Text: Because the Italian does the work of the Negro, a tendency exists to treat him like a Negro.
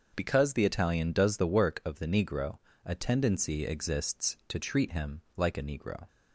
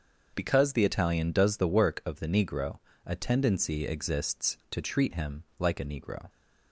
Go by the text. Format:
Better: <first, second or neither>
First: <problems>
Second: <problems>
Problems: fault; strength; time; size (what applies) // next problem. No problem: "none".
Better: neither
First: starts louder than the rest; until 1.1 s; 6 dB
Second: starts louder than the rest; until 1.3 s; 6.5 dB